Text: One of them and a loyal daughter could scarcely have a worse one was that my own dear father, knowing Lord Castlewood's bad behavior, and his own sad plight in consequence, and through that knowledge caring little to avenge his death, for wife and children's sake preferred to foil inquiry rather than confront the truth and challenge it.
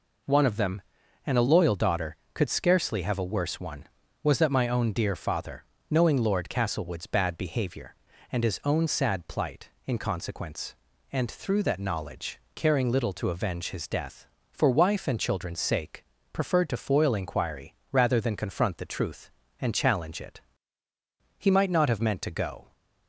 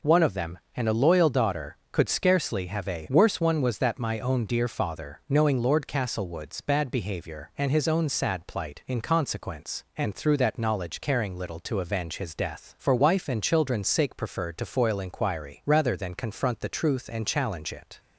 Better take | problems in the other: second | pauses between "knowledge" and "caring"; slight; at 12.3 s; 0.16 s long // pauses between "sake" and "preferred"; slight; at 16.0 s; 0.30 s long // pauses between "inquiry" and "rather"; slight; at 17.7 s; 0.16 s long // goes on to say "He might not have meant to go"; from 21.3 s on; 1.3 s long

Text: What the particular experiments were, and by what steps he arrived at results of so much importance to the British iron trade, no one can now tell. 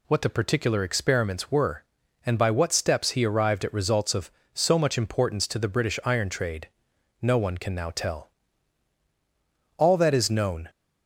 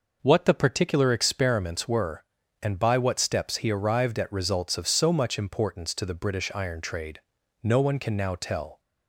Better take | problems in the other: second | goes on to say "All that is known"; noticeable; from 9.8 s on; 0.86 s long

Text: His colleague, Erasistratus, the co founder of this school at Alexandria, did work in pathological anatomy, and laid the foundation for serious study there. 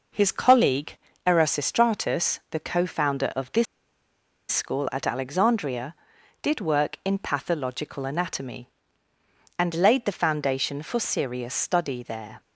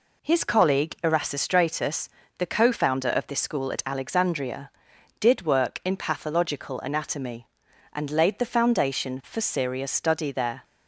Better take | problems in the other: second | pauses between "this" and "school"; noticeable; at 3.6 s; 0.86 s long

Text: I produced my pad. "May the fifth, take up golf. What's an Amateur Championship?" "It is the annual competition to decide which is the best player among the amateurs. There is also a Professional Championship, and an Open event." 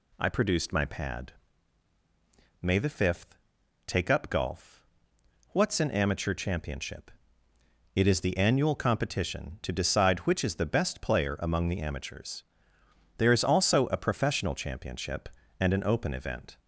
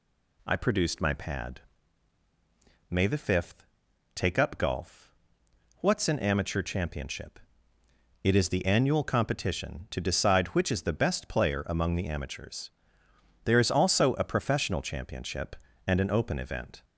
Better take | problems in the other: neither | none

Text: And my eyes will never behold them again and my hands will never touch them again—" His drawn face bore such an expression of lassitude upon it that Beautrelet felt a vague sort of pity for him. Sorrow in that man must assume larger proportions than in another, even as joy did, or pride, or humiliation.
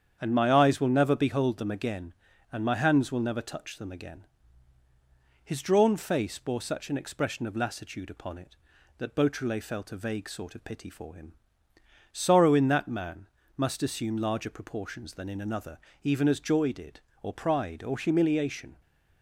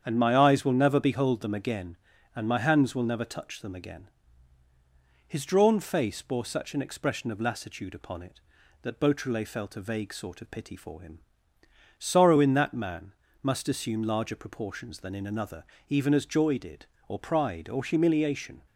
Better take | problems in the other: neither | starts louder than the rest; strong; the same in both // pauses between "man" and "must"; slight; the same in both

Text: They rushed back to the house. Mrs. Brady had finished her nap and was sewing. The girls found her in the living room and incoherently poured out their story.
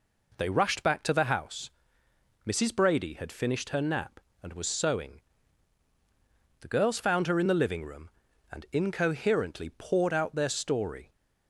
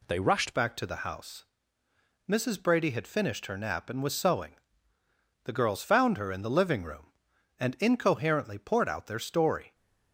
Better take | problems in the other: first | changes voice at "back"; from 0.5 s on; 9.2 s long

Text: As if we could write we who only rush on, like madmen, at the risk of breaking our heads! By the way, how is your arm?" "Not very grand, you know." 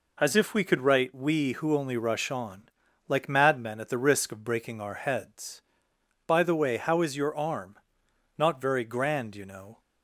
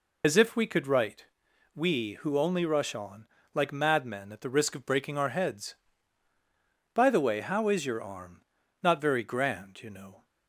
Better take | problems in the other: first | loses the start of "As"; at 0.2 s; 70 ms // pauses between "write" and "we"; noticeable; at 1.2 s; 0.50 s long

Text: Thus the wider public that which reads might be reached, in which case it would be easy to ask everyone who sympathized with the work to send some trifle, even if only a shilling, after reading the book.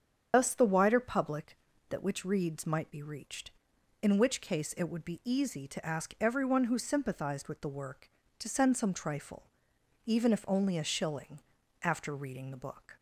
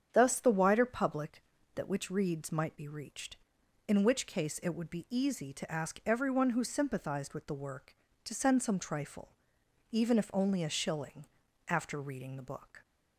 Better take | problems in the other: second | loses the start of "Thus"; at 0.3 s; 80 ms // starts louder than the rest; strong; until 1.3 s; 7.5 dB; strong in the second

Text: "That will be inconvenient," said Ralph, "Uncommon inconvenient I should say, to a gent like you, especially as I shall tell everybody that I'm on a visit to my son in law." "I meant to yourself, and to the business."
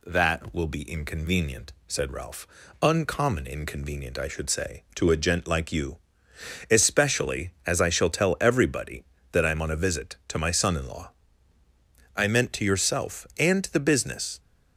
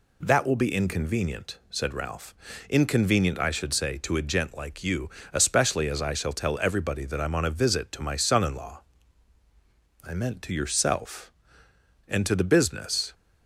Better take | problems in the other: first | skips "Uncommon"; at 2.5 s

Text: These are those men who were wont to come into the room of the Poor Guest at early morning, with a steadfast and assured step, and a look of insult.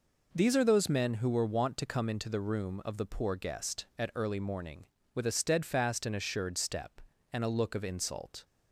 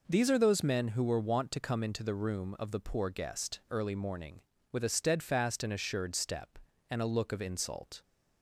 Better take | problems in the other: first | skips "at"; at 3.6 s

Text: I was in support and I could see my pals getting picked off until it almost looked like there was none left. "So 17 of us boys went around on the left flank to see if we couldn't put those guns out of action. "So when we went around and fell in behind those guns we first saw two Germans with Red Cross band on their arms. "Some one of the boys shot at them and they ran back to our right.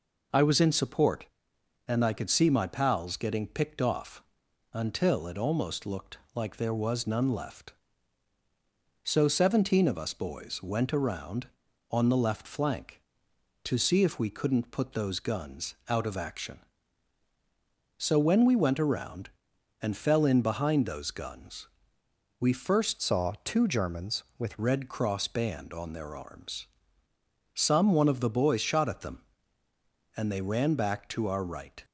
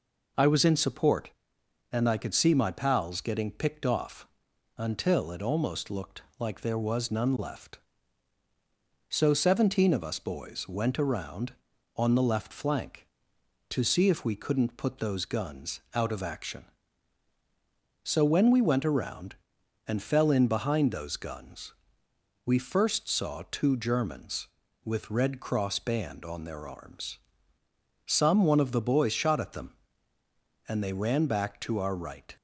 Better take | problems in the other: second | pauses between "off" and "until"; noticeable; at 4.2 s; 0.50 s long; noticeable in the second // pauses between "looked" and "like"; slight; at 6.1 s; 0.18 s long; slight in the second // pauses between "guns" and "we"; noticeable; at 21.6 s; 0.72 s long; noticeable in the second // changes voice from "saw" to "with"; from 22.9 to 24.5 s; 1.6 s long

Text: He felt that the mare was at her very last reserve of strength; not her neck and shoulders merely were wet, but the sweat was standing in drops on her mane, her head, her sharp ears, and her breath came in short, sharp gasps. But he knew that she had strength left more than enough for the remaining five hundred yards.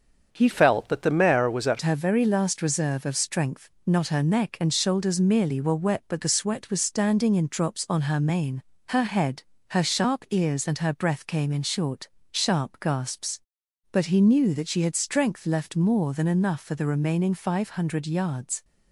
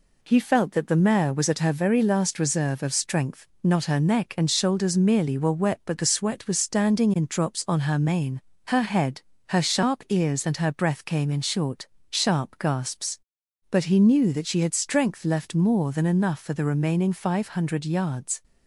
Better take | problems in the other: second | starts louder than the rest; until 1.3 s; 7 dB // changes voice from "felt" to "at"; from 0.5 to 1.7 s; 1.2 s long

